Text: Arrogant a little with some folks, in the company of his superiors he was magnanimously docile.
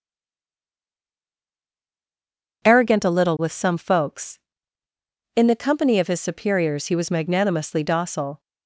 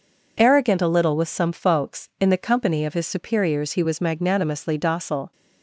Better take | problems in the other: second | stays silent before the first word; strong; until 2.6 s; 2.6 s long

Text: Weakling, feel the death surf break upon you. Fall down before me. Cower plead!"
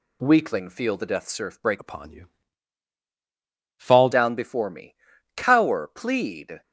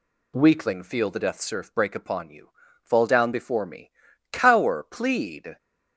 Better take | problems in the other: second | changes voice from "upon" to "Fall"; from 1.7 to 4.0 s; 2.3 s long

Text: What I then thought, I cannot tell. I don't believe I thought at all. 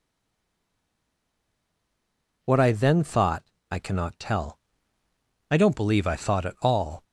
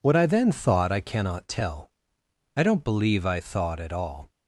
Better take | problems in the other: second | stays silent before the first word; until 2.4 s; 2.4 s long

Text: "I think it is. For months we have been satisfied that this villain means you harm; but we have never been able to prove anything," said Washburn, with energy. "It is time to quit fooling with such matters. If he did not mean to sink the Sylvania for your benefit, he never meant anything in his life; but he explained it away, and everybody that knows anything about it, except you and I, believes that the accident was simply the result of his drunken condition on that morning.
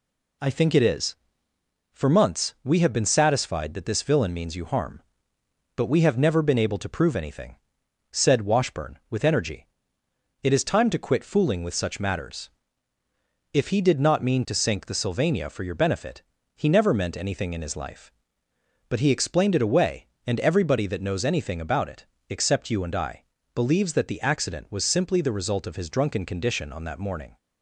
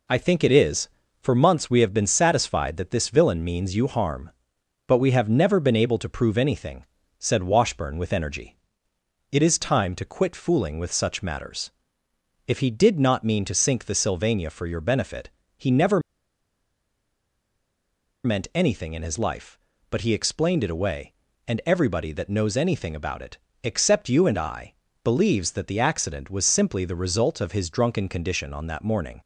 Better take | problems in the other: first | pauses between "never" and "meant"; strong; at 16.0 s; 2.2 s long

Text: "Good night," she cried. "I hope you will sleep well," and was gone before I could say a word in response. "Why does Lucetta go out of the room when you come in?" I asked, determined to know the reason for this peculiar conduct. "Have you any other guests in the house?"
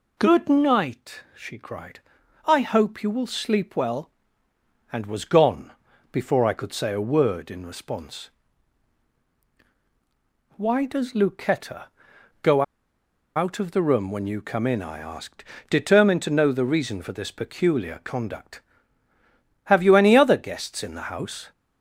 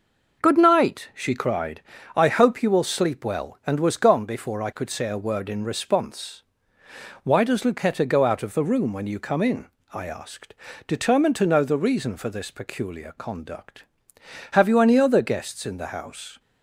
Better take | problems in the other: second | pauses between "gone" and "before"; at 5.7 s; 0.40 s long // pauses between "Lucetta" and "go"; noticeable; at 11.8 s; 0.56 s long // pauses between "go" and "out"; noticeable; at 12.6 s; 0.73 s long

